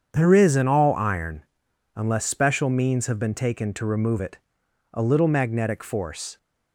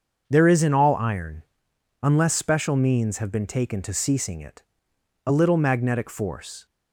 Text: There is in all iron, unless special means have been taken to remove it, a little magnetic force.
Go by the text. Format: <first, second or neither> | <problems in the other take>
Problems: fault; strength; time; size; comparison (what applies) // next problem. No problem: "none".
first | starts louder than the rest; until 1.2 s; 6.5 dB; strong in the first // says "ceasing" for "remove"; at 3.9 s